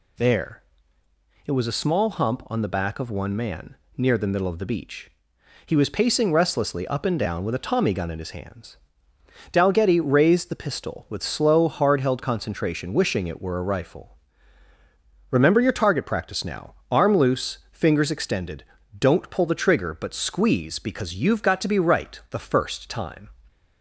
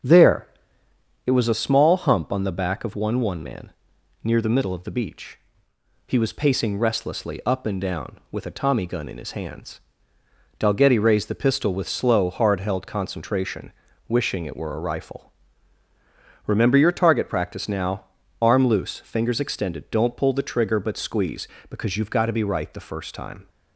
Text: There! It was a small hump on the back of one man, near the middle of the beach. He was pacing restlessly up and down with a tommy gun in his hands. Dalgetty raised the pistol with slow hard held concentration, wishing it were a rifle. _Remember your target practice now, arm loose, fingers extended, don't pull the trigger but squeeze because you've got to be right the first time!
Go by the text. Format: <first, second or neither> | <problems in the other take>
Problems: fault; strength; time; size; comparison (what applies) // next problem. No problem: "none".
first | starts louder than the rest; strong; until 1.8 s; 7.5 dB // says "one" twice; at 3.1 s